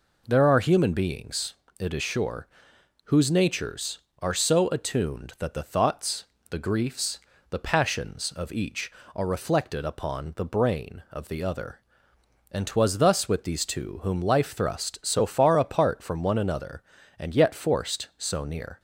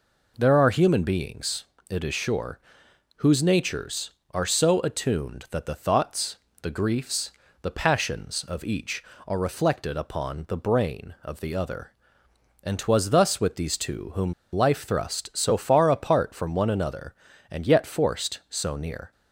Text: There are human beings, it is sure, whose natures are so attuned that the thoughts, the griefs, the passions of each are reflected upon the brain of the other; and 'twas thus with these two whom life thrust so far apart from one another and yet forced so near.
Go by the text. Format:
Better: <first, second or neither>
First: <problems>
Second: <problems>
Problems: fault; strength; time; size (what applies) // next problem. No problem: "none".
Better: first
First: none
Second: pauses between "whom" and "life"; slight; at 14.3 s; 0.20 s long